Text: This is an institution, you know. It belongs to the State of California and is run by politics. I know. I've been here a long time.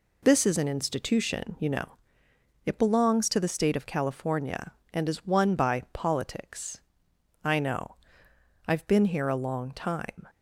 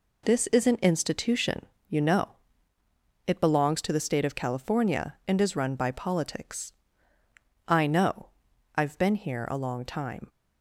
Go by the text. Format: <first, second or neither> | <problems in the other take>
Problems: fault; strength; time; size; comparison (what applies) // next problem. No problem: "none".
second | says "won" for "run"; at 5.2 s